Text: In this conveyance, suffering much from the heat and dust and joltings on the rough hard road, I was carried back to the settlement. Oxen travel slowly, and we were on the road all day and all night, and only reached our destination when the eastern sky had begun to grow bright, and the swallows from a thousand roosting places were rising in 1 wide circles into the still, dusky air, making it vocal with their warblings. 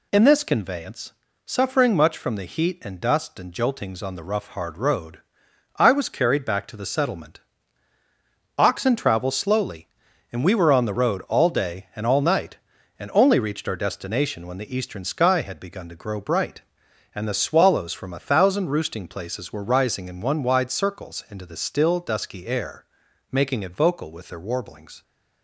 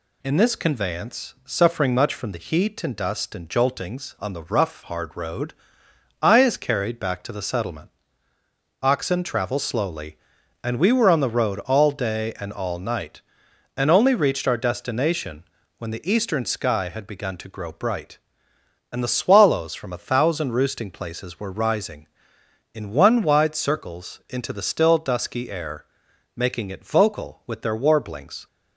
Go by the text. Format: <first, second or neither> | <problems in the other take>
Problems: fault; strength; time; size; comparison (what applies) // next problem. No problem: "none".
first | says "is" for "was"; at 6.4 s // pauses between "destination" and "when"; slight; at 15.4 s; 0.36 s long